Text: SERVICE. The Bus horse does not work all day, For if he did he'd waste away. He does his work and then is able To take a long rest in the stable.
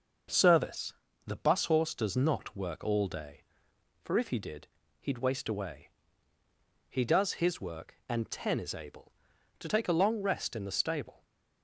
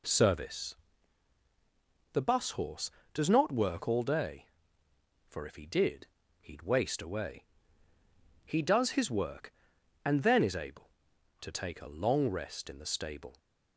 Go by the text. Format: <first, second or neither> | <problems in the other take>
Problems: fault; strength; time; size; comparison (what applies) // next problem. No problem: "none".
second | starts louder than the rest; noticeable; until 1.6 s; 6 dB // pauses between "did" and "he'd"; slight; at 4.6 s; 0.34 s long; slight in the second // says "ten" for "then"; at 8.2 s